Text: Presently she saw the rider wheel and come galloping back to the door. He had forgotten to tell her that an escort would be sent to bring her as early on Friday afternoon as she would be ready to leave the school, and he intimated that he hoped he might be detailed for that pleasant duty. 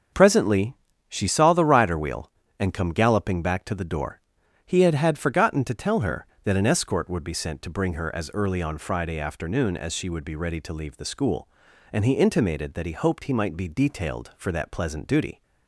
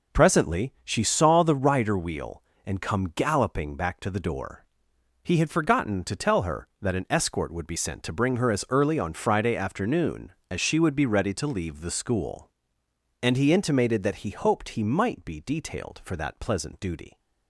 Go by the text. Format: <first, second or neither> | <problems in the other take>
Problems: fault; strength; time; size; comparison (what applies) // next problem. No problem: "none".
second | starts louder than the rest; until 1.4 s; 7 dB // pauses between "Presently" and "she"; slight; at 0.7 s; 0.34 s long // says "had" twice; at 4.9 s